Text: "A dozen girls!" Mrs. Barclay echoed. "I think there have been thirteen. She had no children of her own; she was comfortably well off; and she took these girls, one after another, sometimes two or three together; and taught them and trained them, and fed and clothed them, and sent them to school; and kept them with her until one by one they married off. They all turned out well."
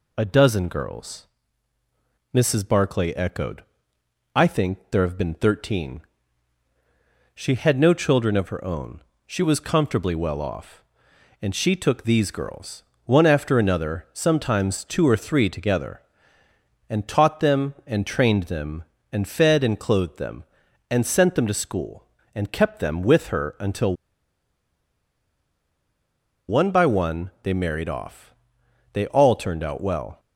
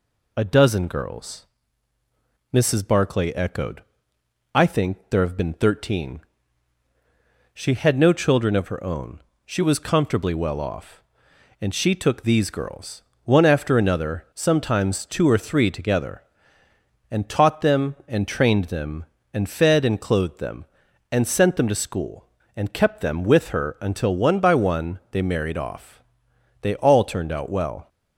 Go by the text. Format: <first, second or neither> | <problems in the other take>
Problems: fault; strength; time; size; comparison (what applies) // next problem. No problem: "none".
second | pauses between "until" and "one"; strong; at 23.9 s; 2.5 s long